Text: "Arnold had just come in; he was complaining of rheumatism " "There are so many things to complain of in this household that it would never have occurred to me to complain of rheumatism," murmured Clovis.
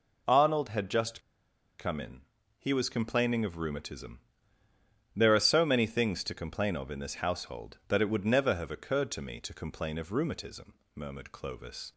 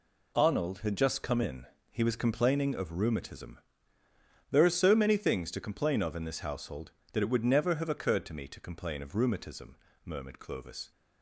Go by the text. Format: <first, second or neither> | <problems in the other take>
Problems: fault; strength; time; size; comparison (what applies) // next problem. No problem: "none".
second | pauses between "just" and "come"; noticeable; at 1.2 s; 0.57 s long